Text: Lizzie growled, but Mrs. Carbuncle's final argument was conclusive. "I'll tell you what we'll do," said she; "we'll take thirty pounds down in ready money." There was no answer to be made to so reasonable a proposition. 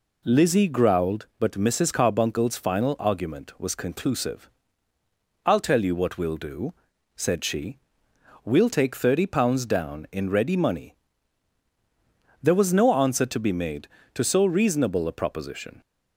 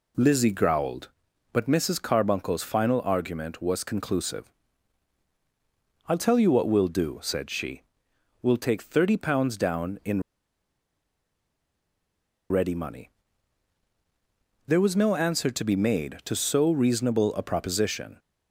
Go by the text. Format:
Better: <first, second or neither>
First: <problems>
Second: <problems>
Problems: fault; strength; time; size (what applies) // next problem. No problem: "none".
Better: first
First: none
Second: pauses between "in" and "ready"; strong; at 10.2 s; 2.2 s long